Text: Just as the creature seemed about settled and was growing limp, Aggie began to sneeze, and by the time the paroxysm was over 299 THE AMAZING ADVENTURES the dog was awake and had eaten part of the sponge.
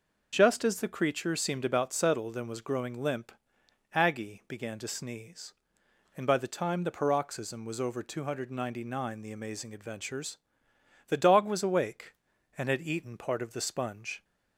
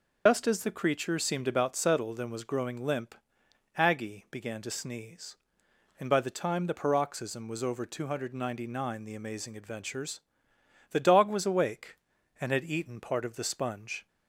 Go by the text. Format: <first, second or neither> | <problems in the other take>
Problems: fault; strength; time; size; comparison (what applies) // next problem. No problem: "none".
first | loses the start of "Just"; at 0.2 s; 100 ms // pauses between "ADVENTURES" and "the"; noticeable; at 10.2 s; 0.68 s long; noticeable in the first